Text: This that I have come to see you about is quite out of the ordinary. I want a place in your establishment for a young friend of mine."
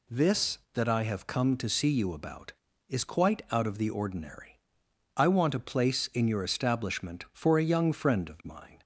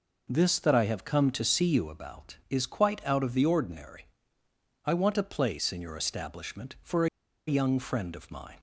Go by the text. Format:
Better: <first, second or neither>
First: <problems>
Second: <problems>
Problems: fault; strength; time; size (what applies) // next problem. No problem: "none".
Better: first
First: none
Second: pauses between "for" and "a"; at 7.0 s; 0.40 s long